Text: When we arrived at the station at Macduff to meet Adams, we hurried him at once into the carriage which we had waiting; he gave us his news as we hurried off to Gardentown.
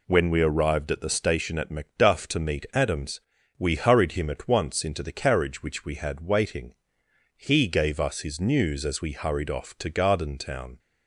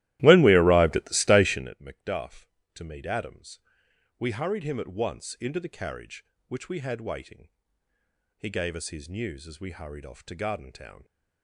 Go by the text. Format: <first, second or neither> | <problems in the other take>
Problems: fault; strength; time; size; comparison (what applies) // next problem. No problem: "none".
first | starts louder than the rest; strong; until 1.8 s; 16 dB